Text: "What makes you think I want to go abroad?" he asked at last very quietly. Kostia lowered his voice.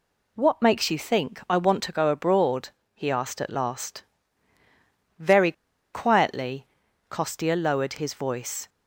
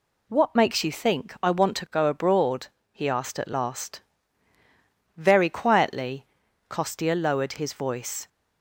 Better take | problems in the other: second | pauses between "last" and "very"; at 4.0 s; 1.1 s long; also in the second // pauses between "very" and "quietly"; at 5.5 s; 0.41 s long

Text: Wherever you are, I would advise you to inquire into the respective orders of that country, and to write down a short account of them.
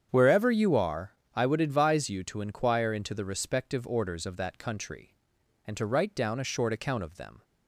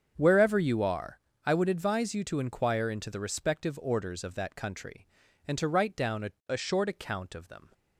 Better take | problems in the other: first | starts louder than the rest; until 1.1 s; 7 dB; strong in the first // says "a" twice; at 6.4 s

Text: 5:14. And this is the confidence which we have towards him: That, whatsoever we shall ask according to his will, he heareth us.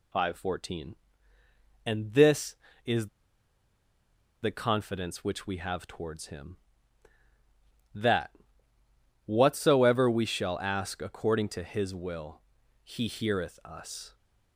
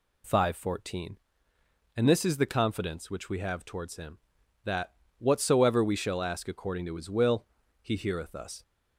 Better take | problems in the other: second | pauses between "is" and "the"; strong; at 3.0 s; 1.3 s long

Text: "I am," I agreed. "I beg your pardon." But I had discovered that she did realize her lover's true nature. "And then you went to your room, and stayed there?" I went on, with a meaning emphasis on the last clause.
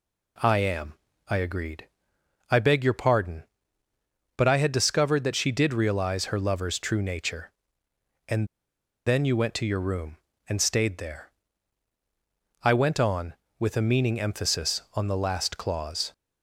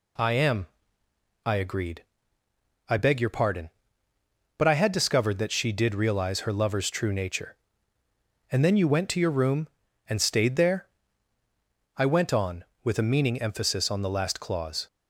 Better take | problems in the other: second | pauses between "And" and "then"; noticeable; at 8.4 s; 0.61 s long

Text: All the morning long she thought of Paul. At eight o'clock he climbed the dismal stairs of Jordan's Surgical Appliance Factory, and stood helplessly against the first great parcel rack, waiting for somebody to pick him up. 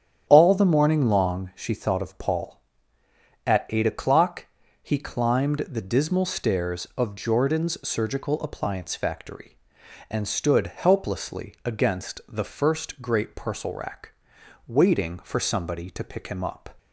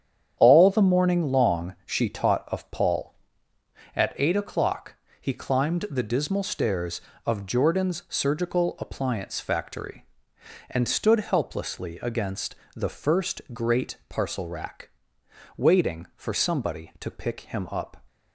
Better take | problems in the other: first | starts louder than the rest; strong; until 1.3 s; 8.5 dB; strong in the first // says "taught" for "thought"; at 2.0 s // pauses between "o'clock" and "he"; slight; at 4.9 s; 0.26 s long; slight in the first // pauses between "against" and "the"; slight; at 12.5 s; 0.18 s long

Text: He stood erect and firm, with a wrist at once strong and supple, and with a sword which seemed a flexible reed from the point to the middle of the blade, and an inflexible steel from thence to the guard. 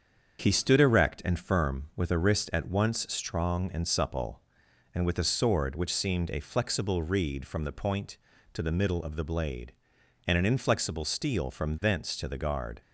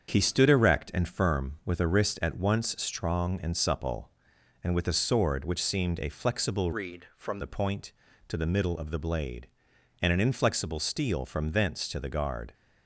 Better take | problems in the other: first | starts louder than the rest; strong; until 1.1 s; 7.5 dB; strong in the first // changes voice from "reed" to "from"; from 6.7 to 7.3 s; 0.6 s long

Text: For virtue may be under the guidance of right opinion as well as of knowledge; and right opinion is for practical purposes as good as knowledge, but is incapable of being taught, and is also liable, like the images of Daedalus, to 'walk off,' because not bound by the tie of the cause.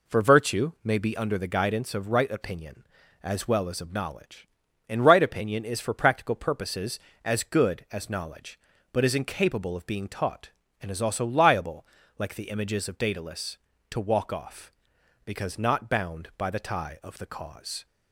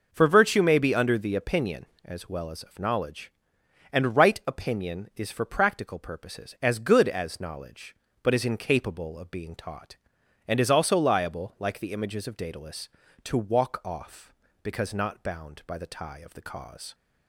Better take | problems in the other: first | skips "guidance of right"; at 1.3 s

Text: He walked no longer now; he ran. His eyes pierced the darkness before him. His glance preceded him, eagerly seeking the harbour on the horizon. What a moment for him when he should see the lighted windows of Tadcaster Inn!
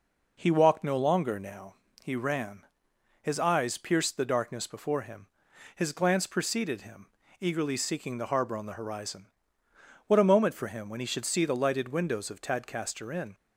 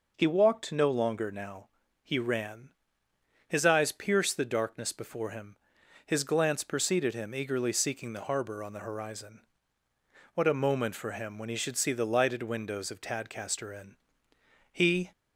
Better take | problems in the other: first | goes on to say "He"; slight; from 14.7 s on; 0.40 s long

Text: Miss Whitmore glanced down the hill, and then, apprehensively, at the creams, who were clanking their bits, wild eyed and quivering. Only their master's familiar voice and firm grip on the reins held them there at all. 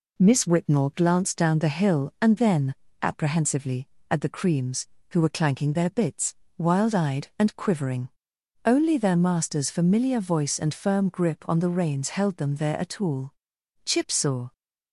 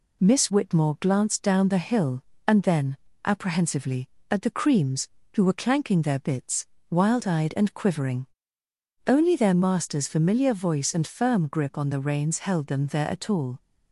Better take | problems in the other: second | goes on to say "Chip saw"; noticeable; from 13.8 s on; 0.68 s long

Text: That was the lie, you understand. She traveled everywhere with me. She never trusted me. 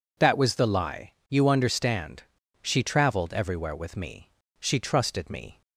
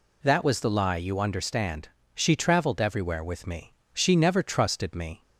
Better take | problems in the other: second | skips "never"; at 4.7 s

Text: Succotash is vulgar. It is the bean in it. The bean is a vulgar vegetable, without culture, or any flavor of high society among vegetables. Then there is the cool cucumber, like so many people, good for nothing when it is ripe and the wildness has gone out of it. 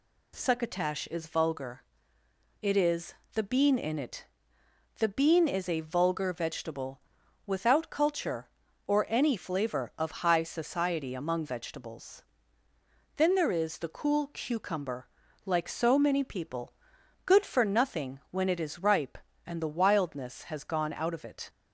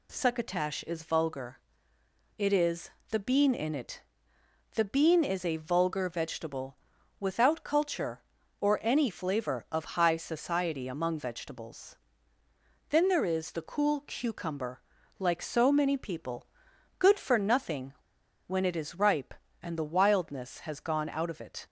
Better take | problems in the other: first | pauses between "is" and "the"; slight; at 2.9 s; 0.20 s long; slight in the first // pauses between "nothing" and "when"; noticeable; at 17.9 s; 0.52 s long

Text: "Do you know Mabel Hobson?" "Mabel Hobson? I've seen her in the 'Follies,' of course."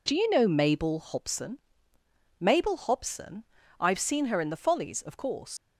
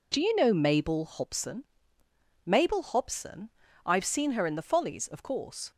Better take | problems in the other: second | leaves "course" unfinished; at 5.5 s; 80 ms

